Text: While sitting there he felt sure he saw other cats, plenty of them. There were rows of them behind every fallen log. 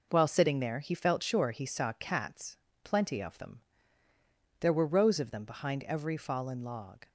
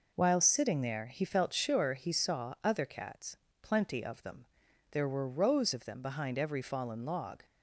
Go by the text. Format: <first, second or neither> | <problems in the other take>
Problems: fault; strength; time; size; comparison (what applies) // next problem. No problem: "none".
second | skips "other"; at 1.9 s